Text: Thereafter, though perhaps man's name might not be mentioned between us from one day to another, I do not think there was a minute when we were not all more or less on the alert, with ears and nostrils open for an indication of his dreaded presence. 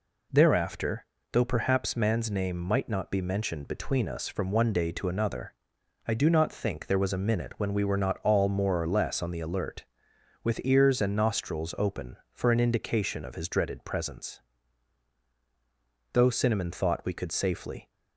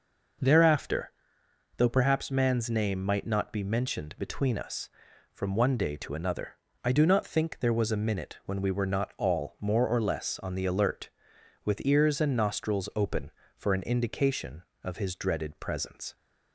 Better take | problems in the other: second | goes on to say "Though Cinnamon thought we could safely"; strong; from 16.1 s on; 1.7 s long

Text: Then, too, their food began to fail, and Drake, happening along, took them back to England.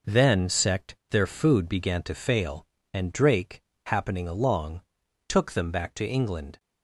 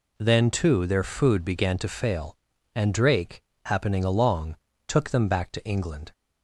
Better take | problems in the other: second | says "sect" for "too"; at 0.4 s

